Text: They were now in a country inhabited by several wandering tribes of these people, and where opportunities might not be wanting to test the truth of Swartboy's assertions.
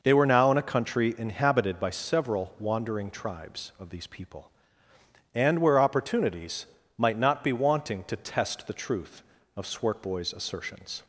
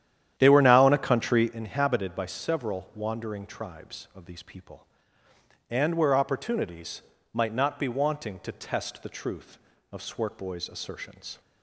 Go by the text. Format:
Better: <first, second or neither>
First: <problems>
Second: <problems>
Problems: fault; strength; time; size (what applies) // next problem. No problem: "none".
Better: first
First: pauses between "opportunities" and "might"; slight; at 6.6 s; 0.32 s long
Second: starts louder than the rest; strong; until 1.5 s; 10.5 dB // pauses between "opportunities" and "might"; slight; at 7.0 s; 0.32 s long